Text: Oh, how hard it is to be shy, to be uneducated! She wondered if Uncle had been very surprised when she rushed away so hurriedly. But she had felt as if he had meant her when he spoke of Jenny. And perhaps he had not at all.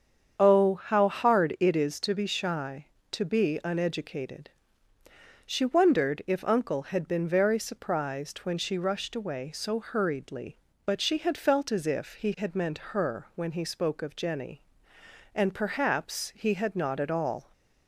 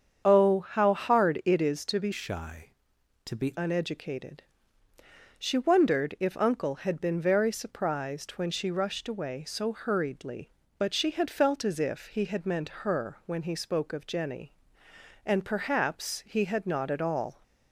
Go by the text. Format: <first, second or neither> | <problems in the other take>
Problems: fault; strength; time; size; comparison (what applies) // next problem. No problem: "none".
first | starts louder than the rest; strong; until 1.2 s; 7.5 dB; strong in the first // changes voice from "shy" to "be"; from 2.1 to 3.5 s; 1.4 s long